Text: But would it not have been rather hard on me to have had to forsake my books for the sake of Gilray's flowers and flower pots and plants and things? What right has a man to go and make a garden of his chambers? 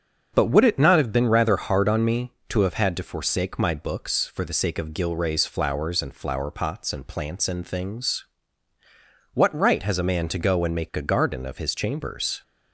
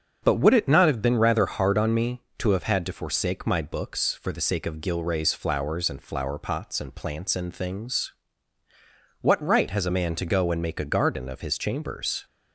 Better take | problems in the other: neither | starts louder than the rest; strong; the same in both

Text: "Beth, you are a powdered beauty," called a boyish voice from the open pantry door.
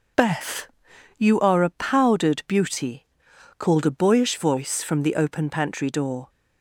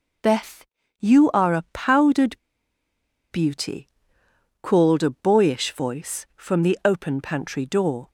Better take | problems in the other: first | pauses between "powdered" and "beauty"; noticeable; at 2.3 s; 0.96 s long

